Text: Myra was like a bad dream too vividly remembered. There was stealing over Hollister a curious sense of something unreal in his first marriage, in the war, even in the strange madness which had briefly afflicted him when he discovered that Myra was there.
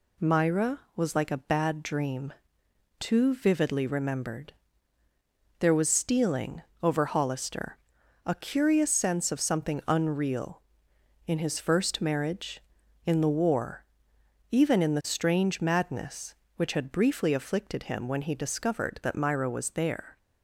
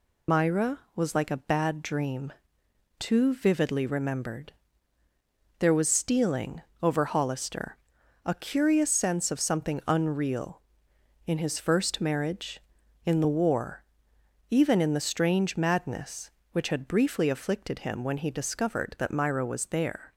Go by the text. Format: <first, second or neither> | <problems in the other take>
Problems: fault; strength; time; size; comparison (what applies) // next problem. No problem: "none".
first | loses the start of "Myra"; at 0.2 s; 90 ms // pauses between "dream" and "too"; noticeable; at 2.3 s; 0.66 s long; noticeable in the first // pauses between "stealing" and "over"; slight; at 6.6 s; 0.20 s long; slight in the first // pauses between "Hollister" and "a"; noticeable; at 7.7 s; 0.48 s long; noticeable in the first